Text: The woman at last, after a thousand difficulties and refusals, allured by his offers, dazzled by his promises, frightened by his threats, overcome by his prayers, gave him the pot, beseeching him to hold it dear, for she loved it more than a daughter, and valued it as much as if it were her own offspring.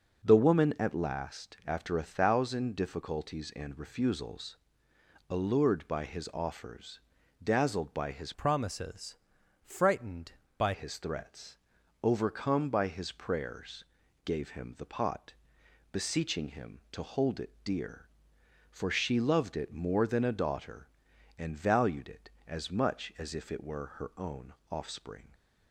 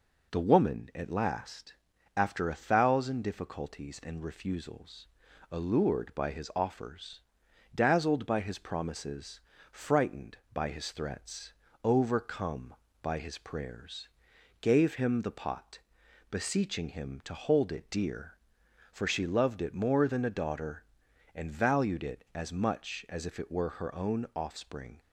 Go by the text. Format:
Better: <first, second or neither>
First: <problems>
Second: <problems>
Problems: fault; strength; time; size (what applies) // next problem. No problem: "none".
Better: second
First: changes voice from "promises" to "by"; from 8.3 to 10.7 s; 2.4 s long // pauses between "own" and "offspring"; slight; at 24.5 s; 0.16 s long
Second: none